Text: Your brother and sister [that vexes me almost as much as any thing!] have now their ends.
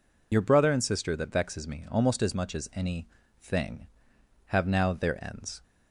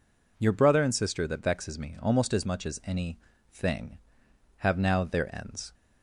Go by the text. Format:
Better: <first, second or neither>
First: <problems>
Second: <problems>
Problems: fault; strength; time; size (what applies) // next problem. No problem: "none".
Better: second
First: loses the start of "Your"; at 0.3 s; 50 ms // pauses between "any" and "thing"; slight; at 3.0 s; 0.30 s long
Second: pauses between "any" and "thing"; slight; at 3.1 s; 0.30 s long